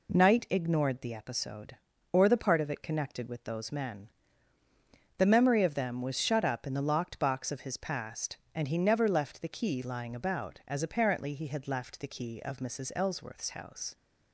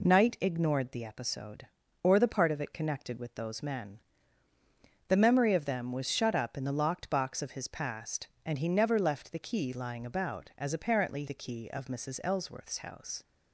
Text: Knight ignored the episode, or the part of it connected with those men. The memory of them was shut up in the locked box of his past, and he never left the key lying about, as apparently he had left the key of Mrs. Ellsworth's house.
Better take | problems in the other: first | skips "he had left"; at 11.2 s

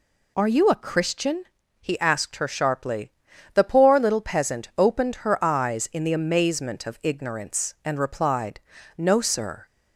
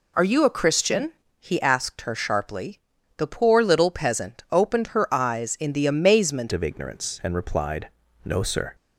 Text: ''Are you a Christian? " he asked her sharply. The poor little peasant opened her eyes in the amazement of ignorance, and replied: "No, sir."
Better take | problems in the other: first | changes voice at "of"; from 6.5 s on; 2.2 s long

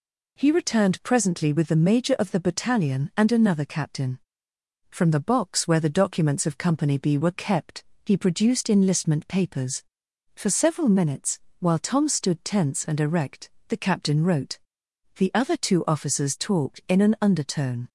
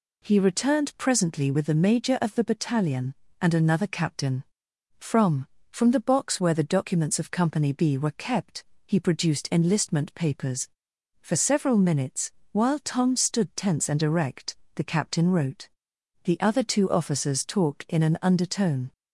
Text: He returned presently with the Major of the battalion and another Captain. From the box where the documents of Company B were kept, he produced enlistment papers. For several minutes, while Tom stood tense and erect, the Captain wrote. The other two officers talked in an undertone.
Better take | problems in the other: first | says "From" twice; at 5.7 s

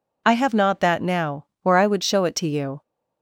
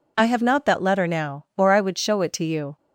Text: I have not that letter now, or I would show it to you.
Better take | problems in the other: second | skips "letter"; at 1.0 s

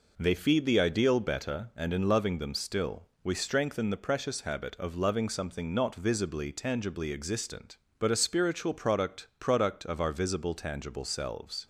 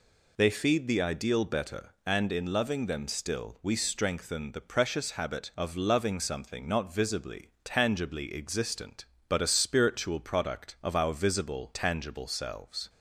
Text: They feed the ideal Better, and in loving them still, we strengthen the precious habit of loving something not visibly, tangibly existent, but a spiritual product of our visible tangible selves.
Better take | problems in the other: second | says "product" twice; at 9.4 s

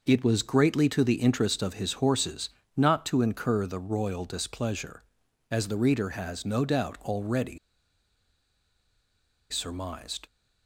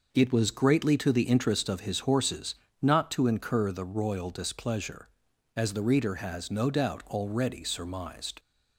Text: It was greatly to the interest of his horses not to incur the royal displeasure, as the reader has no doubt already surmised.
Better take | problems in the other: second | pauses between "horses" and "not"; slight; at 2.4 s; 0.26 s long; slight in the second // pauses between "already" and "surmised"; strong; at 7.5 s; 1.9 s long

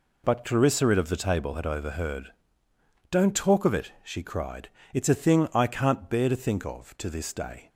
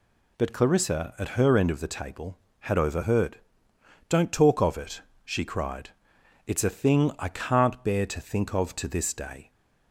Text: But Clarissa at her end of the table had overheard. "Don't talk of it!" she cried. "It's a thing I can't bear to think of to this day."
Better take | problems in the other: second | skips "her end"; at 0.9 s

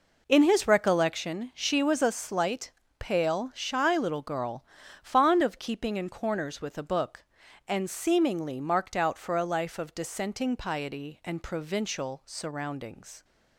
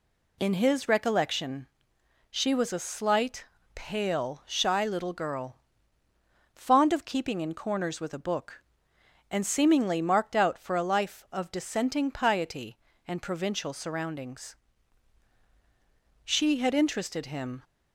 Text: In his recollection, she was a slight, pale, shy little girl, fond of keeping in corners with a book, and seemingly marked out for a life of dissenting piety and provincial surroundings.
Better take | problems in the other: first | goes on to say "She had interested him"; from 16.2 s on; 1.3 s long

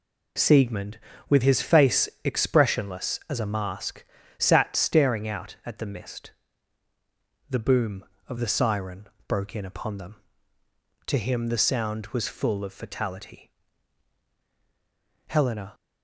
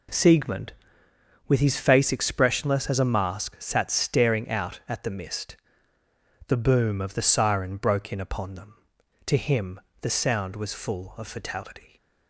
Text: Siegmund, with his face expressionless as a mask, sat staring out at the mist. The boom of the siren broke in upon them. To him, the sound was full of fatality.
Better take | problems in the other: second | pauses between "siren" and "broke"; slight; at 9.0 s; 0.20 s long // goes on to say "Helena"; slight; from 15.2 s on; 0.48 s long

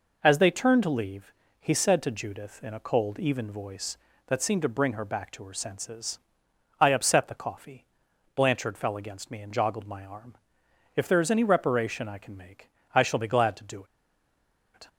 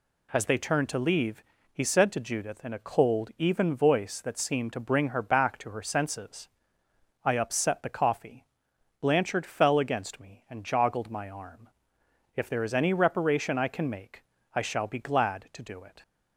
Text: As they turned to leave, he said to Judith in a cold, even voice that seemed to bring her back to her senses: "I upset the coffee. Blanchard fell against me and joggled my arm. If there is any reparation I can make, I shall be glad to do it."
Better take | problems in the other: second | pauses between "do" and "it"; noticeable; at 13.8 s; 0.89 s long

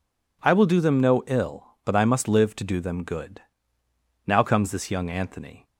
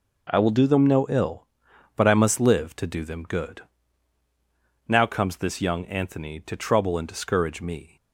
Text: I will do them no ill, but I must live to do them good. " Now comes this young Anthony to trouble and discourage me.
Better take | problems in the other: second | stops before "to trouble and discourage me"; at 5.6 s

